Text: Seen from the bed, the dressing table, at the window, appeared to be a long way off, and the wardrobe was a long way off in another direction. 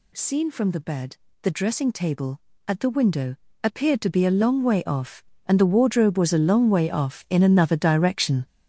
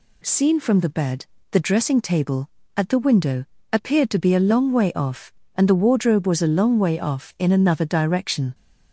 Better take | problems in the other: second | gets louder; strong; throughout; 8.5 dB

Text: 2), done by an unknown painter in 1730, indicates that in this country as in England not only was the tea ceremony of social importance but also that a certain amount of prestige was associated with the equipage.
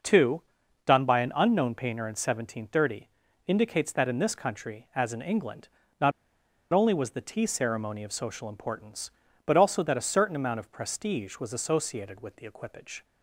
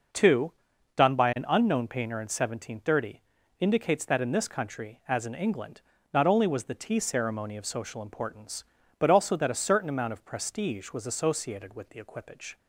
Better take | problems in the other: second | pauses between "England" and "not"; slight; at 5.6 s; 0.34 s long; slight in the second // pauses between "not" and "only"; noticeable; at 6.1 s; 0.62 s long

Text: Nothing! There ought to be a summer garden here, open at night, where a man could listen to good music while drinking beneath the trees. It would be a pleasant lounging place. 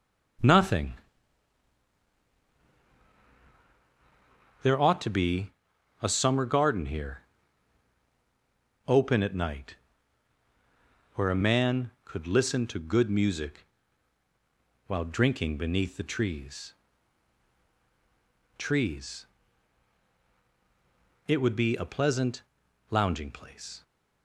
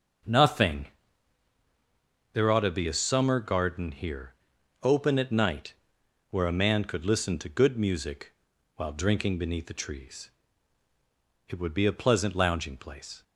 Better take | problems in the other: second | starts louder than the rest; strong; until 5.1 s; 7.5 dB; also in the second // pauses between "be" and "a"; noticeable; at 5.4 s; 0.52 s long // pauses between "music" and "while"; at 13.6 s; 1.2 s long; also in the second // says "trees" twice; at 18.5 s // pauses between "pleasant" and "lounging"; noticeable; at 22.4 s; 0.48 s long

